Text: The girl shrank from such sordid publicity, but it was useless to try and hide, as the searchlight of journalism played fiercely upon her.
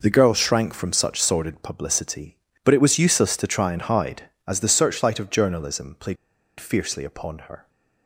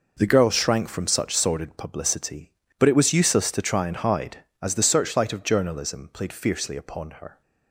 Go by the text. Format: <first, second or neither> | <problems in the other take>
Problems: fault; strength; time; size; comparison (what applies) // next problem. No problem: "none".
second | pauses between "played" and "fiercely"; at 6.1 s; 0.42 s long